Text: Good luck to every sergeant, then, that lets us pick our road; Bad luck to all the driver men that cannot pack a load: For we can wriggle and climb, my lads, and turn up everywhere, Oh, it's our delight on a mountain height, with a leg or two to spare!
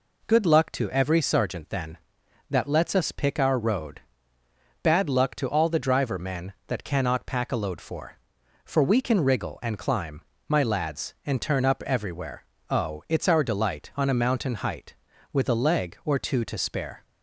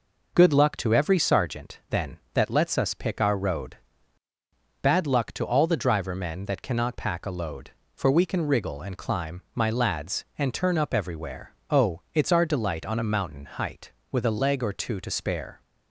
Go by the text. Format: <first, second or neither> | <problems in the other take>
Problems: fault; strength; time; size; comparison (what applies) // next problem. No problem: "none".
second | says "For" twice; at 8.6 s